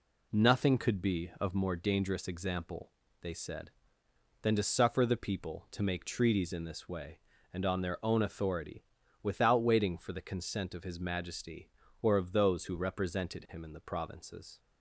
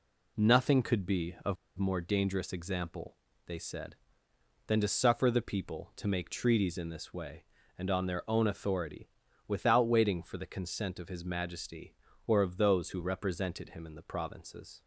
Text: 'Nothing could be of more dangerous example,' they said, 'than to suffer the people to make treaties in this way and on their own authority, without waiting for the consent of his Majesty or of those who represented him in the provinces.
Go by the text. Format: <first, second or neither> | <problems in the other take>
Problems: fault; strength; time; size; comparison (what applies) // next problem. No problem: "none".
first | pauses between "of" and "more"; slight; at 1.5 s; 0.23 s long